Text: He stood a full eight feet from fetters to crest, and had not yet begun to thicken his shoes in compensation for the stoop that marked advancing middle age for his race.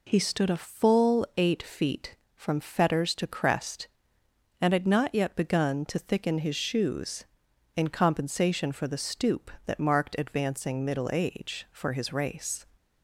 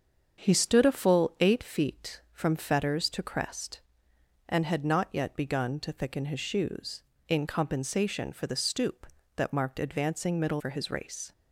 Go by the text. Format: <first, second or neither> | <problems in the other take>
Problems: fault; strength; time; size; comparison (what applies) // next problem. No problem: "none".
first | starts louder than the rest; strong; until 1.4 s; 7 dB // skips "age"; at 10.5 s